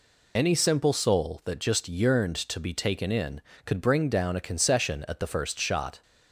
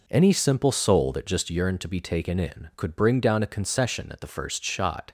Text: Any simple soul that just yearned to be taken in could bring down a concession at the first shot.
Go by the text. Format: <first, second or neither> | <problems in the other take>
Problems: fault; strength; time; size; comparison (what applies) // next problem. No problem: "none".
second | loses the start of "Any"; at 0.3 s; 35 ms